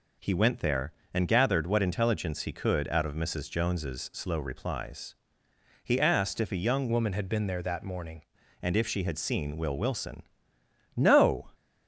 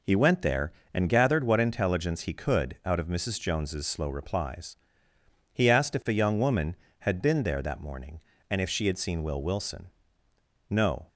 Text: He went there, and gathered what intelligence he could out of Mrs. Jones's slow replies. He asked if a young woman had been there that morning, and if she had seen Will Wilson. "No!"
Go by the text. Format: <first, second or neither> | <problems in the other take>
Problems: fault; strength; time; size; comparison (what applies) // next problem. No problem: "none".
second | changes voice from "woman" to "morning"; from 6.9 to 8.2 s; 1.3 s long